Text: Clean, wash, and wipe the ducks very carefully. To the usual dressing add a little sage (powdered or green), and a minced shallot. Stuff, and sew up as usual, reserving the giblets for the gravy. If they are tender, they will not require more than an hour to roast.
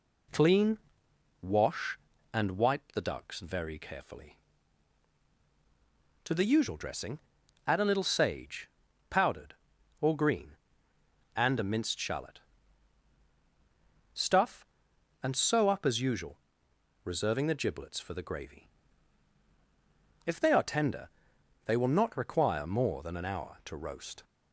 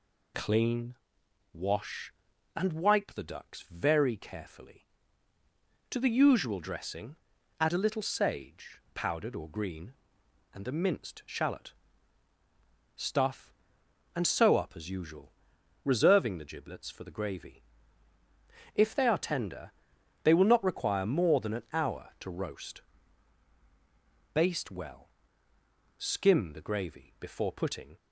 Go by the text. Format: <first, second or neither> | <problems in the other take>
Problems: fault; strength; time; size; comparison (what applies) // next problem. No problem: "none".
first | pauses between "dressing" and "add"; at 7.1 s; 0.42 s long; noticeable in the first // goes on to say "Baste well Skim the gravy before putting"; strong; from 24.3 s on; 3.6 s long